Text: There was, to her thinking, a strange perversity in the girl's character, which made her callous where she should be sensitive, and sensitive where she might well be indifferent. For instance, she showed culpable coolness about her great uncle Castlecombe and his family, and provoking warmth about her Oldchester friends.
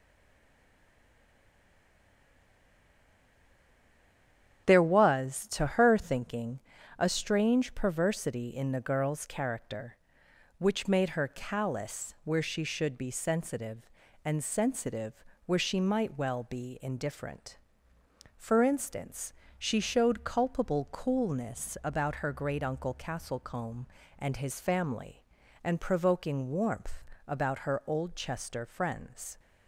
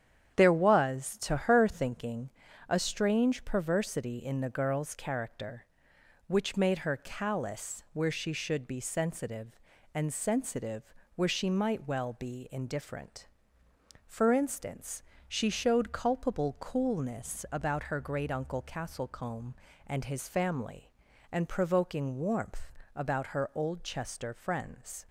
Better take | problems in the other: second | stays silent before the first word; strong; until 4.6 s; 4.6 s long // starts louder than the rest; strong; until 5.7 s; 9.5 dB; strong in the second // pauses between "sensitive" and "where"; slight; at 15.2 s; 0.22 s long; slight in the second // pauses between "warmth" and "about"; slight; at 27.0 s; 0.24 s long; slight in the second

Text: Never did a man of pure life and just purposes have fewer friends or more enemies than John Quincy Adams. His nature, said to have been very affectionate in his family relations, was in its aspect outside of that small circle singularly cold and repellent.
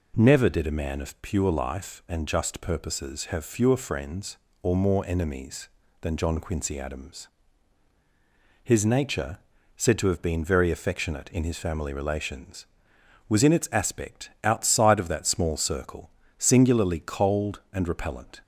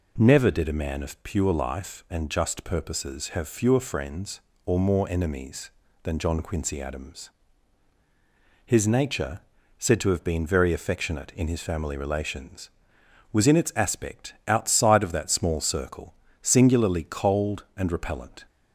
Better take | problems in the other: neither | pauses between "circle" and "singularly"; slight; the same in both

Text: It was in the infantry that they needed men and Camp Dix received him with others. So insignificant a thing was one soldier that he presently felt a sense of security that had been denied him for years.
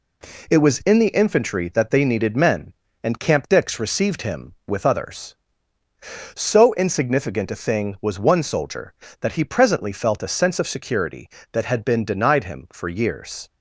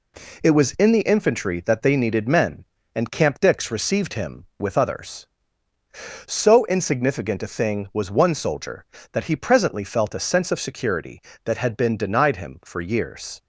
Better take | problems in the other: neither | none

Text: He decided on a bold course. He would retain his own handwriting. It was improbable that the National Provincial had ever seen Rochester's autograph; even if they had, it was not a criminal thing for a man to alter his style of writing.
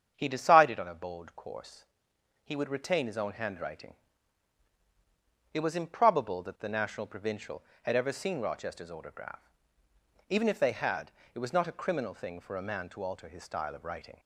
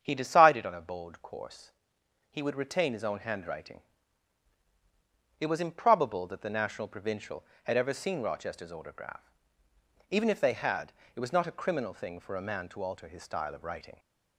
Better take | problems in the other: neither | starts louder than the rest; strong; the same in both

